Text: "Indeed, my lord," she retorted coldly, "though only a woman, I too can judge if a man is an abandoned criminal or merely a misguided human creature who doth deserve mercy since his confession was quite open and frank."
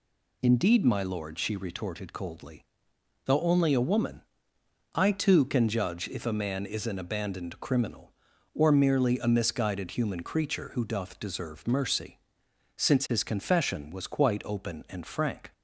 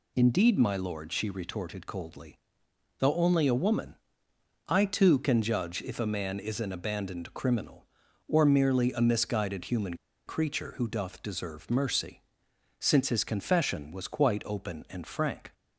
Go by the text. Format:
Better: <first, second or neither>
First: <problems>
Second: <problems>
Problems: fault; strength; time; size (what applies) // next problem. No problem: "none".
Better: first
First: pauses between "mercy" and "since"; noticeable; at 12.1 s; 0.58 s long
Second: pauses between "human" and "creature"; slight; at 9.9 s; 0.31 s long // pauses between "mercy" and "since"; noticeable; at 12.2 s; 0.58 s long